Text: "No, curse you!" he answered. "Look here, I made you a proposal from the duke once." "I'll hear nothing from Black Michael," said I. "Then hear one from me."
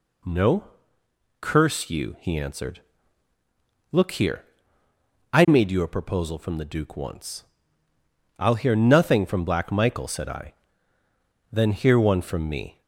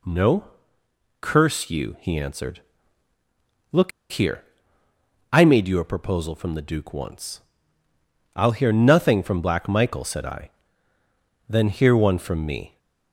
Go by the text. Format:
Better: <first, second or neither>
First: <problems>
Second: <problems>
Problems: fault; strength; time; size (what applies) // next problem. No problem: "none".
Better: first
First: none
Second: pauses between "Look" and "here"; slight; at 3.9 s; 0.21 s long